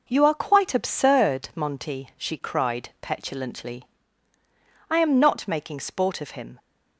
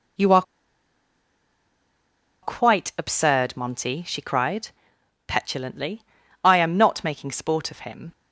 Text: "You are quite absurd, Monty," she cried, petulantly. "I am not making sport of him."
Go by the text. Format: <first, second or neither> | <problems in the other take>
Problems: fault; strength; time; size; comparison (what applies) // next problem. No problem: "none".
first | pauses between "are" and "quite"; strong; at 0.4 s; 2.0 s long